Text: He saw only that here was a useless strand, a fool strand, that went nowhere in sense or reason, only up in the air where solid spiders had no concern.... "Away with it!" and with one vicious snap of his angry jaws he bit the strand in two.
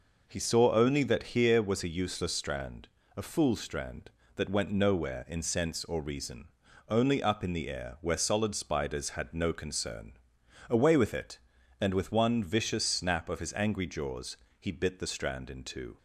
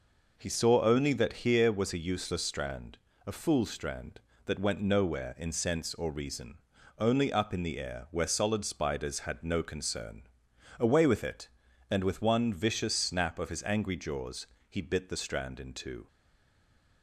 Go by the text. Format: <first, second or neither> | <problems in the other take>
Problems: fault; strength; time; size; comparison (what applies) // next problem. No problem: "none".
first | pauses between "jaws" and "he"; slight; at 14.4 s; 0.24 s long; slight in the first // stays silent after the last word; slight; from 16.0 s on; 1.0 s long